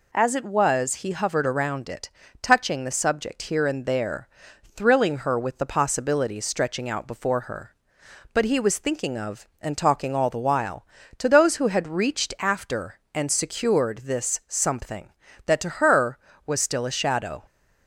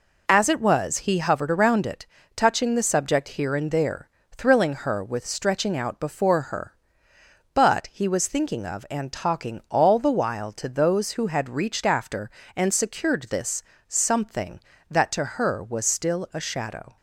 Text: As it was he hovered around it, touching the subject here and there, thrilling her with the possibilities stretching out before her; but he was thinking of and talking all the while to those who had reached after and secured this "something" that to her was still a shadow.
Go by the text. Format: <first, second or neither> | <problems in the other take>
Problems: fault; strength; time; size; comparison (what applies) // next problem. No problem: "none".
first | skips "the possibilities"; at 5.2 s // pauses between "this" and "something"; slight; at 13.6 s; 0.24 s long